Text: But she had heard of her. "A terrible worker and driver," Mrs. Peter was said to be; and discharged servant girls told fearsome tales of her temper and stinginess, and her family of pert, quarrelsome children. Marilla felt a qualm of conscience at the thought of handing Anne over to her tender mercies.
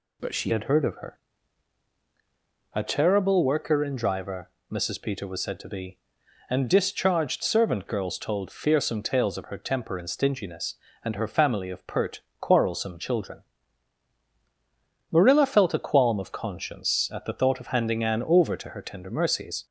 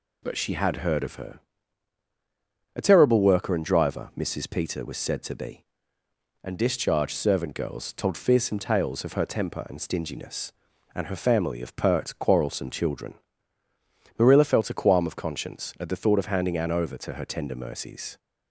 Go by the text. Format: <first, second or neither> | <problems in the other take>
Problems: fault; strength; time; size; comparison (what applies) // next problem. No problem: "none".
second | changes voice at "had"; from 0.4 s on; 19.2 s long